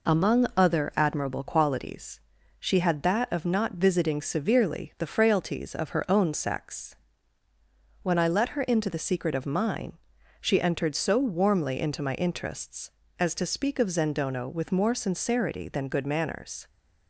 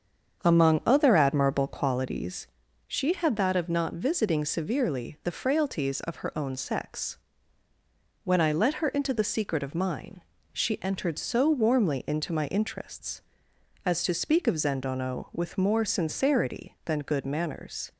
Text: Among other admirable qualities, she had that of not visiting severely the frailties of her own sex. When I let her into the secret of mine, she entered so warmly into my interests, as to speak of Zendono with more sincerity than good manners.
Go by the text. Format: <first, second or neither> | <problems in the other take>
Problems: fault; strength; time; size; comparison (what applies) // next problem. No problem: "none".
first | starts louder than the rest; strong; until 2.0 s; 7.5 dB